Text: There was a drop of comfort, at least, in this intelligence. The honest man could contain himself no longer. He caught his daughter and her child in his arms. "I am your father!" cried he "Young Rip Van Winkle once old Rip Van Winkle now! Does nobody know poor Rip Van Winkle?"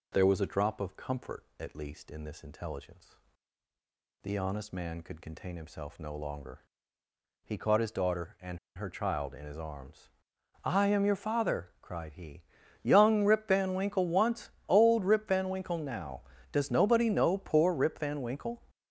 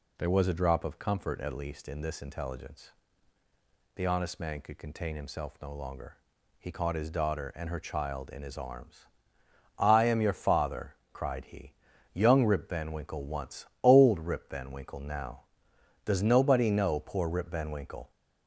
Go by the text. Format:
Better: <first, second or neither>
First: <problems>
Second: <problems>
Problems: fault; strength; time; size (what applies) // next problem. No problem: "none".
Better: second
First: pauses between "and" and "her"; slight; at 8.5 s; 0.18 s long // pauses between "he" and "Young"; at 12.4 s; 0.38 s long // pauses between "once" and "old"; slight; at 14.5 s; 0.18 s long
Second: pauses between "he" and "Young"; at 11.7 s; 0.40 s long // pauses between "once" and "old"; slight; at 13.6 s; 0.18 s long